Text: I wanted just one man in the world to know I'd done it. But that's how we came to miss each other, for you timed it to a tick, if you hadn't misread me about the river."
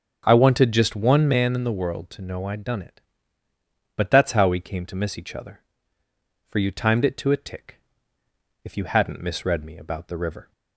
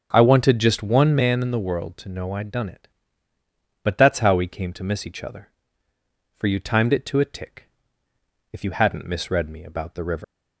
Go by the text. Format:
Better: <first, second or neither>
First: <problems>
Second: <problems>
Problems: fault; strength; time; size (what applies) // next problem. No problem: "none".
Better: first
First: starts louder than the rest; until 1.2 s; 7 dB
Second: starts louder than the rest; until 1.1 s; 7 dB // leaves "river" unfinished; at 10.2 s; 140 ms